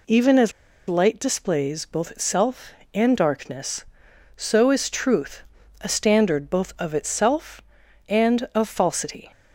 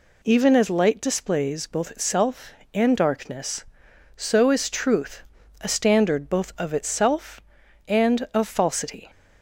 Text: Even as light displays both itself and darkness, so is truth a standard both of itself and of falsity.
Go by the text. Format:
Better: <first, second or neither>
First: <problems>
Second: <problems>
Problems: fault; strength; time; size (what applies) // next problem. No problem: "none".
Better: second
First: pauses between "as" and "light"; at 0.5 s; 0.36 s long // pauses between "truth" and "a"; at 5.4 s; 0.40 s long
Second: pauses between "truth" and "a"; at 5.2 s; 0.40 s long